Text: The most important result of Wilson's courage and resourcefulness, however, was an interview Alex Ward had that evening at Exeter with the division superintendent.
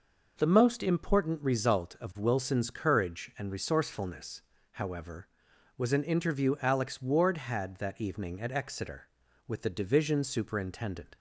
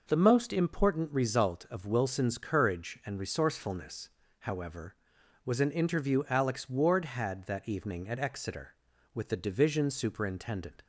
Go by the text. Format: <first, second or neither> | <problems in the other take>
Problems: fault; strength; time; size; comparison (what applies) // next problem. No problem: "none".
neither | none